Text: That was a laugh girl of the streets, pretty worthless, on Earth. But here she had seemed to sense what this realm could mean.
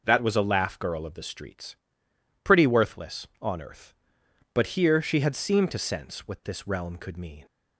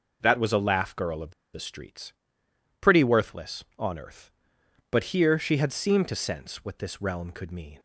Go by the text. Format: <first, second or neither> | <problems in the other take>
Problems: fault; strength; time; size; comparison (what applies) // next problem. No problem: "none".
first | pauses between "of" and "the"; slight; at 1.3 s; 0.22 s long